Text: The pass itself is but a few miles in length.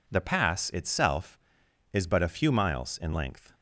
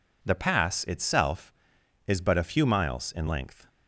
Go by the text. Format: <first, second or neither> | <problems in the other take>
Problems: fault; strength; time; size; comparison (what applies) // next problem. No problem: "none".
neither | none